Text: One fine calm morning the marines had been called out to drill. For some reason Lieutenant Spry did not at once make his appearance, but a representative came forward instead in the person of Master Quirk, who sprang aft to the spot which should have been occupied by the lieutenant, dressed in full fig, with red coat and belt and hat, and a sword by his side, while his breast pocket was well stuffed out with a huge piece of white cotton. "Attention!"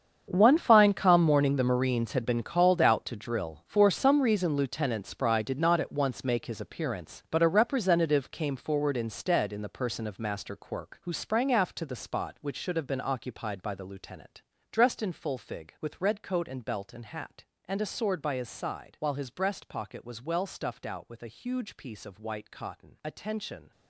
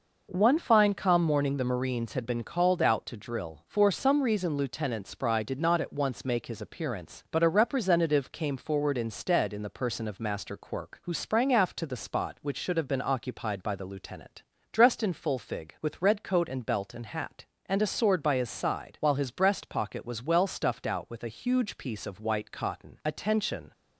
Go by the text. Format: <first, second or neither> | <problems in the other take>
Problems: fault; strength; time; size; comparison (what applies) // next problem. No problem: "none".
second | gets quieter; strong; throughout; 16 dB